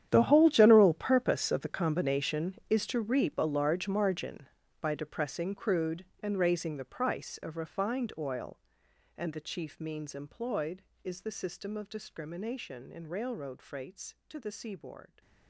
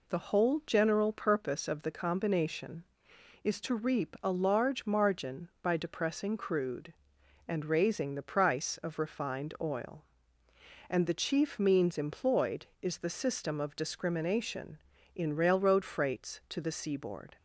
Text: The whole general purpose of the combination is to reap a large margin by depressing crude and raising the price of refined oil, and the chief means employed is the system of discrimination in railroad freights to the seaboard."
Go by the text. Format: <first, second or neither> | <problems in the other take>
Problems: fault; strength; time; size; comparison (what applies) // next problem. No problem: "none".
second | gets quieter; strong; throughout; 17 dB